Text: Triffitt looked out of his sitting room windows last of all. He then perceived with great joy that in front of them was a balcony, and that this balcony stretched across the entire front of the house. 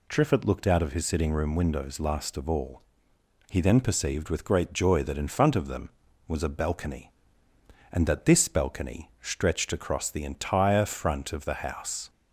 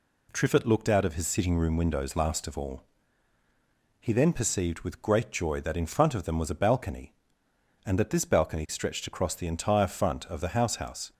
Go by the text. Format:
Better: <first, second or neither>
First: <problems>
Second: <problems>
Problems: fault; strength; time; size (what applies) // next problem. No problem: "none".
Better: first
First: none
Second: says "house" twice; at 10.7 s